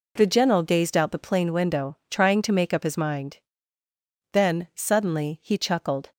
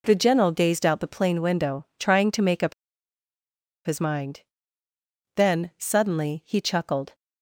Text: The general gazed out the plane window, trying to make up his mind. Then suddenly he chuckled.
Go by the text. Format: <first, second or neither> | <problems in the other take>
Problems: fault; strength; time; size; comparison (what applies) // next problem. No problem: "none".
first | pauses between "up" and "his"; at 2.7 s; 1.1 s long